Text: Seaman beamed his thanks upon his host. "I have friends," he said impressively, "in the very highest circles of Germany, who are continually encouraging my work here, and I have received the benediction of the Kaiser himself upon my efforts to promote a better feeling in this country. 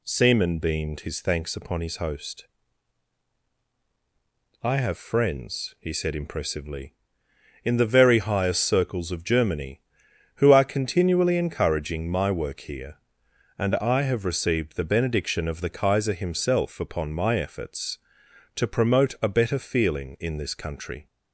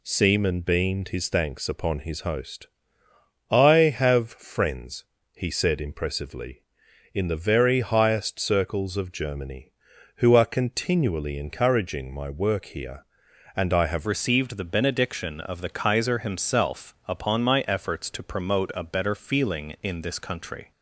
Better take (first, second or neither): first